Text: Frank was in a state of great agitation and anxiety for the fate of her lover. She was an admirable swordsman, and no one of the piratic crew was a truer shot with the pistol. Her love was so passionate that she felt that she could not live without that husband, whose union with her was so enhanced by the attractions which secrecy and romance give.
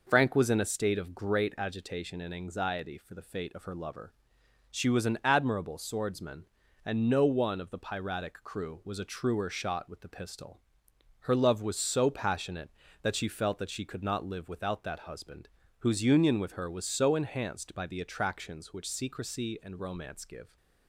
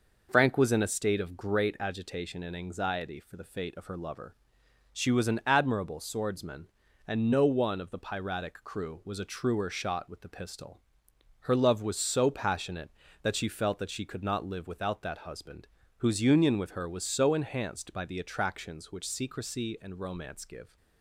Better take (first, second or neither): neither